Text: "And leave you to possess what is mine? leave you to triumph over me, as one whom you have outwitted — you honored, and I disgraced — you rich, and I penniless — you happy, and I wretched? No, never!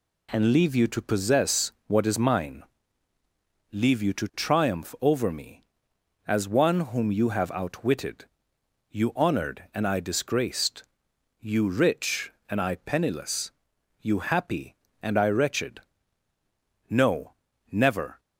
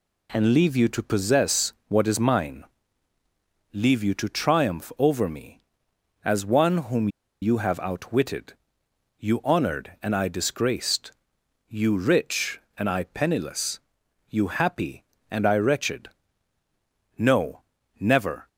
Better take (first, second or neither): first